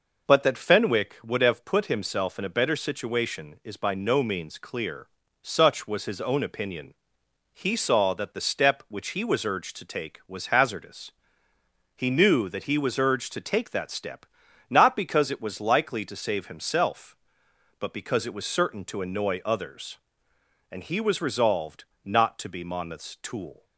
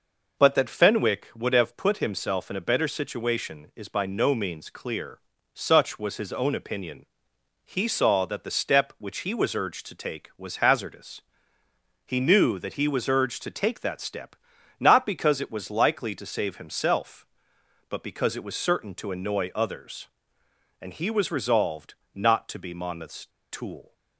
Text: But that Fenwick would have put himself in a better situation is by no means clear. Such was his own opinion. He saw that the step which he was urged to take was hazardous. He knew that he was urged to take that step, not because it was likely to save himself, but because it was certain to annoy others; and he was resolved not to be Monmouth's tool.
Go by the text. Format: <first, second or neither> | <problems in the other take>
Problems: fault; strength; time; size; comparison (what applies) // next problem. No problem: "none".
first | pauses between "resolved" and "not"; slight; at 21.9 s; 0.20 s long; slight in the first // pauses between "Monmouth's" and "tool"; slight; at 23.2 s; 0.24 s long